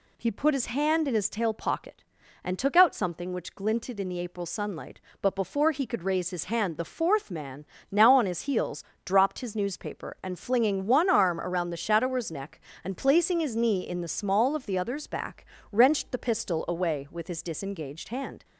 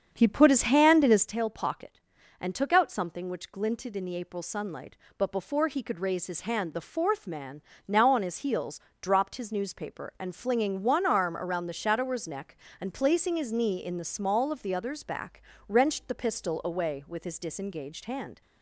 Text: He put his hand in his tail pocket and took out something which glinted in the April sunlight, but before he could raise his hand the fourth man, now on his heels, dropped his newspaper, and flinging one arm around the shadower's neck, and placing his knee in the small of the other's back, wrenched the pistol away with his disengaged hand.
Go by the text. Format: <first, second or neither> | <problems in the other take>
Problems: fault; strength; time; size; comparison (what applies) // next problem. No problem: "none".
first | starts louder than the rest; until 1.3 s; 7 dB